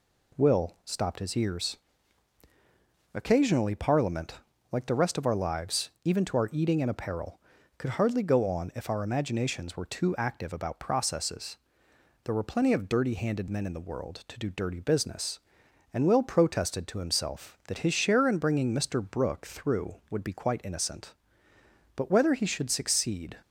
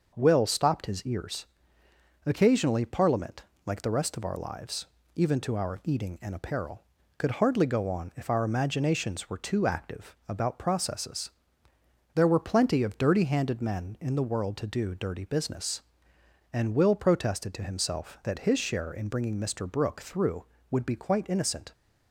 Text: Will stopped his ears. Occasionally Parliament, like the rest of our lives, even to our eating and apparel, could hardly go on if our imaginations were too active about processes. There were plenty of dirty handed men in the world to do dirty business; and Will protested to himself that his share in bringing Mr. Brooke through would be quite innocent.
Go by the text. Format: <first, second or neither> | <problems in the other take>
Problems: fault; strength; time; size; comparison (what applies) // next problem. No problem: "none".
second | goes on to say "But whether he should succeed"; from 21.9 s on; 1.4 s long